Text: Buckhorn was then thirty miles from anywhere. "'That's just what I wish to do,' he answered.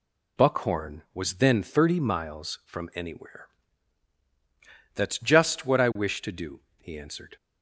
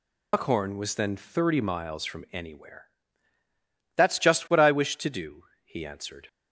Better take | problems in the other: first | loses the start of "Buckhorn"; at 0.3 s; 90 ms

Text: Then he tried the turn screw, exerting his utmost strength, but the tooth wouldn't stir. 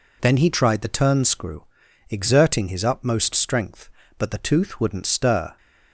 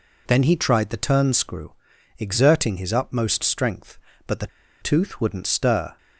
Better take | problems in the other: first | pauses between "the" and "tooth"; slight; at 4.4 s; 0.33 s long

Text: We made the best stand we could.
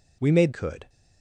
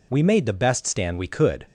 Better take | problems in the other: second | skips "the best stand we"; at 0.5 s

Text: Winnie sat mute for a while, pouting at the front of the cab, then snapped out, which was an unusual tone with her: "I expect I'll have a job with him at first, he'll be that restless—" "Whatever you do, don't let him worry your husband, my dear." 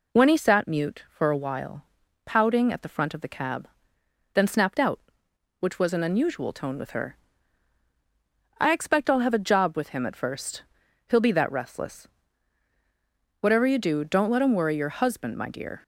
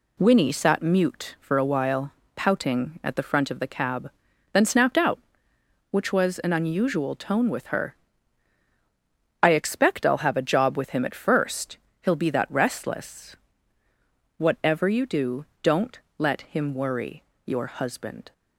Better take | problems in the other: first | pauses between "don't" and "let"; slight; at 16.0 s; 0.18 s long // pauses between "worry" and "your"; slight; at 17.2 s; 0.24 s long // stops before "my dear"; at 18.3 s

